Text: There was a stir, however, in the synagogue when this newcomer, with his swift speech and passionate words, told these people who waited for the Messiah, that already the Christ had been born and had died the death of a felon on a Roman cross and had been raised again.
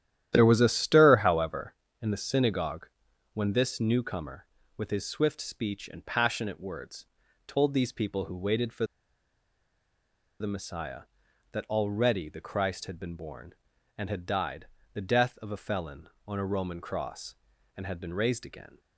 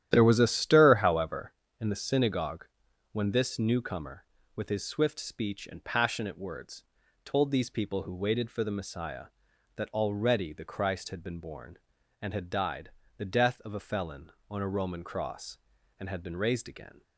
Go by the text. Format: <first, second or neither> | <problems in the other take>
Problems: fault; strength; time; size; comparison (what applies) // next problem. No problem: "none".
second | starts louder than the rest; strong; until 1.3 s; 11 dB; strong in the second // pauses between "synagogue" and "when"; noticeable; at 2.8 s; 0.46 s long; noticeable in the second // pauses between "for" and "the"; strong; at 8.8 s; 1.5 s long // pauses between "died" and "the"; slight; at 14.6 s; 0.26 s long; slight in the second